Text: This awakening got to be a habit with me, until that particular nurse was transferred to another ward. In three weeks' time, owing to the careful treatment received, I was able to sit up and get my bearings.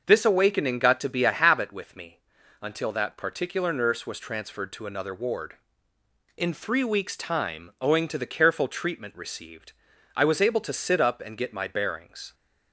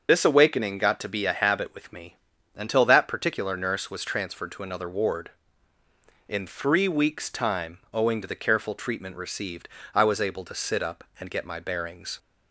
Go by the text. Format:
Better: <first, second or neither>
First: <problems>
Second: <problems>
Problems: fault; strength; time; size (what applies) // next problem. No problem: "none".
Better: first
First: starts louder than the rest; until 1.0 s; 6 dB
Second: loses the start of "This"; at 0.0 s; 50 ms // starts louder than the rest; until 1.1 s; 6.5 dB